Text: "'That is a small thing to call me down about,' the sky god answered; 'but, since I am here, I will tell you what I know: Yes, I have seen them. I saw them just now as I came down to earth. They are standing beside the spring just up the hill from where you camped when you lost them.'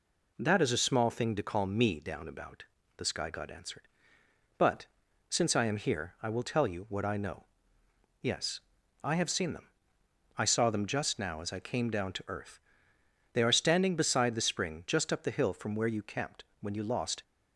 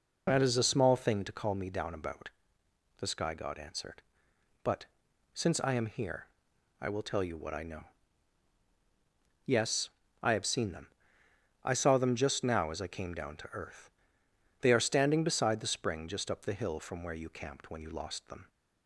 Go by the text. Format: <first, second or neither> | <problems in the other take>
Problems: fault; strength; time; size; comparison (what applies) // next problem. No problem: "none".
second | pauses between "camped" and "when"; slight; at 16.4 s; 0.20 s long // stops before "them"; at 17.2 s